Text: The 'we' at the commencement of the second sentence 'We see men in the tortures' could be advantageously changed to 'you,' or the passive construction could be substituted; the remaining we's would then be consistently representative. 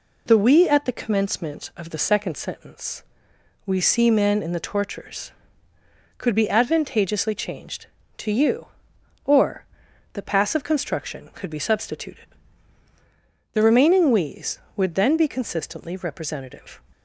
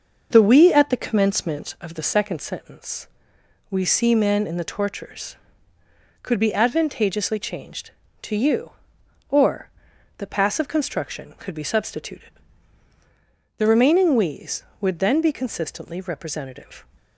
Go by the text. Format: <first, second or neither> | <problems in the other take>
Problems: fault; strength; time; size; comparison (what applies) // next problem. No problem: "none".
first | starts louder than the rest; until 1.9 s; 6 dB // pauses between "sentence" and "We"; noticeable; at 3.0 s; 0.62 s long; noticeable in the first // pauses between "or" and "the"; noticeable; at 9.6 s; 0.50 s long; noticeable in the first